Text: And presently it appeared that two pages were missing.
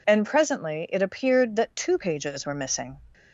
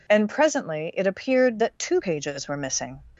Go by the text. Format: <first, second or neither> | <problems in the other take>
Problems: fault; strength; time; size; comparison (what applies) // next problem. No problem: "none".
neither | none